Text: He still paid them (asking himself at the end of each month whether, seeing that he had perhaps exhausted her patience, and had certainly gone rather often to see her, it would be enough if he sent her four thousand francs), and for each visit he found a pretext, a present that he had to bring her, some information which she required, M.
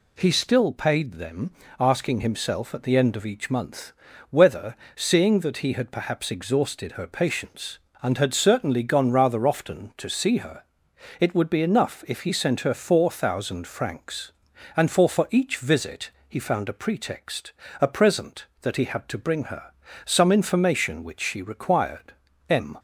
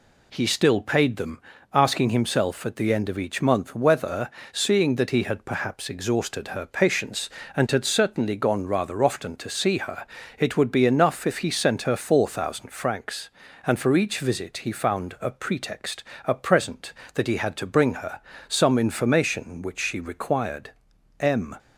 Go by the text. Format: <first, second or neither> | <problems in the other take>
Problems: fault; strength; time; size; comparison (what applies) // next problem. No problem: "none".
second | pauses between "month" and "whether"; at 3.9 s; 0.38 s long // says "for" twice; at 15.0 s // pauses between "visit" and "he"; slight; at 16.1 s; 0.18 s long